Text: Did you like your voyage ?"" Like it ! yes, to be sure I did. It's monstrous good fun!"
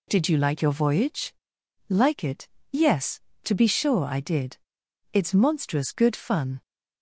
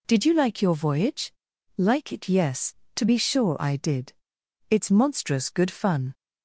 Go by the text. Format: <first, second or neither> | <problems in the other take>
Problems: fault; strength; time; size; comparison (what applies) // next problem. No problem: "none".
neither | none